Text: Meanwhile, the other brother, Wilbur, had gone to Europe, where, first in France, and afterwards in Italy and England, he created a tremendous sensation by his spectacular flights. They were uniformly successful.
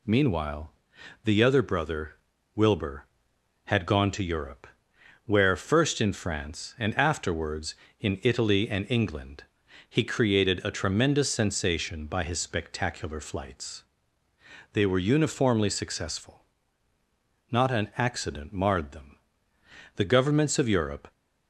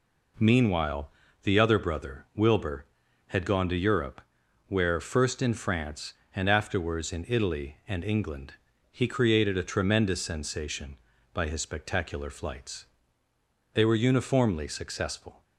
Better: second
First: goes on to say "Not an accident marred them The governments of Europe"; strong; from 17.5 s on; 3.6 s long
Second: none

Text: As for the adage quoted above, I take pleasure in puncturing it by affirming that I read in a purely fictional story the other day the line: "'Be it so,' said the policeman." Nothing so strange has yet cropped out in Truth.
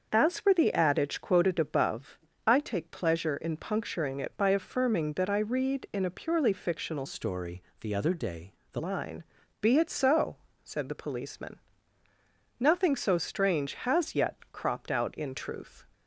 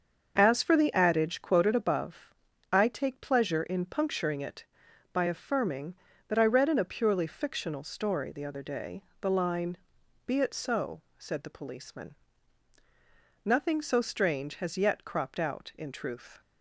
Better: second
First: starts louder than the rest; until 1.1 s; 6.5 dB // changes voice from "story" to "the"; from 7.0 to 8.8 s; 1.8 s long // pauses between "story" and "the"; slight; at 7.6 s; 0.16 s long // pauses between "day" and "the"; slight; at 8.5 s; 0.18 s long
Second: starts louder than the rest; until 1.3 s; 6.5 dB // pauses between "day" and "the"; slight; at 9.0 s; 0.16 s long

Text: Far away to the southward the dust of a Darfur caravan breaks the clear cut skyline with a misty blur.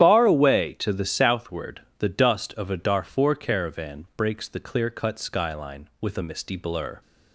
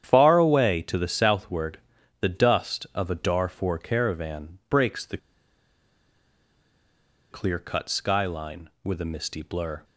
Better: first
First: starts louder than the rest; strong; until 1.0 s; 10 dB // pauses between "southward" and "the"; slight; at 1.8 s; 0.16 s long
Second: starts louder than the rest; strong; until 1.0 s; 9.5 dB // pauses between "southward" and "the"; at 1.7 s; 0.42 s long // pauses between "the" and "clear"; strong; at 5.1 s; 2.1 s long

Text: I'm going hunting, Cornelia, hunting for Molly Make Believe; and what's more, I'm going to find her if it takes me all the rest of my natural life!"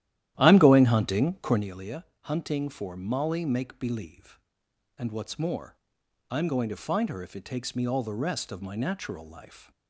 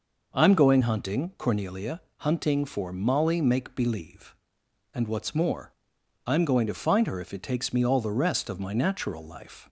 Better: second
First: starts louder than the rest; strong; until 1.7 s; 12.5 dB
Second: none

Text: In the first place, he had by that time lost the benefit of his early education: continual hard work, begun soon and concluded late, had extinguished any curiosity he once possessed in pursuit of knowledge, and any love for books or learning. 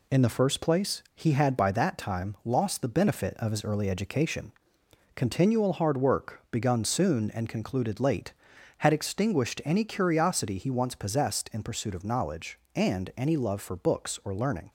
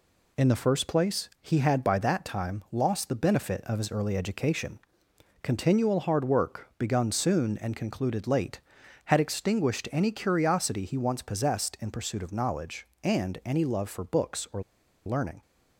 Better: first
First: none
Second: pauses between "or" and "learning"; at 14.6 s; 0.45 s long

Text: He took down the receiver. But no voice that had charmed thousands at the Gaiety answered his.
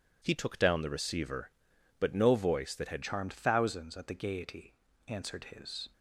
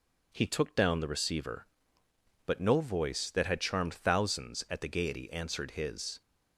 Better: second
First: changes voice at "charmed"; from 3.0 s on; 2.8 s long // pauses between "Gaiety" and "answered"; slight; at 4.7 s; 0.34 s long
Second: none

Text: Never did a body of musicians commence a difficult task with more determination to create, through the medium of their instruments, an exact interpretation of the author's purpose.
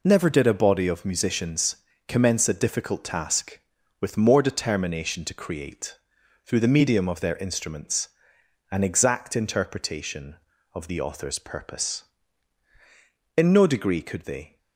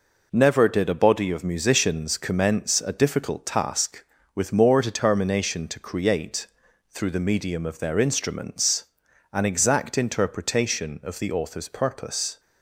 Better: second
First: pauses between "musicians" and "commence"; slight; at 1.7 s; 0.32 s long // goes on to say "In no degree could they"; noticeable; from 13.3 s on; 1.2 s long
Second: none

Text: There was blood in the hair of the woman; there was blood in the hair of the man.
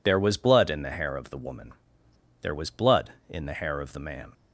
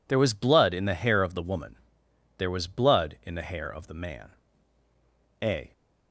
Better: first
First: none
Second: goes on to say "A"; slight; from 5.4 s on; 0.30 s long

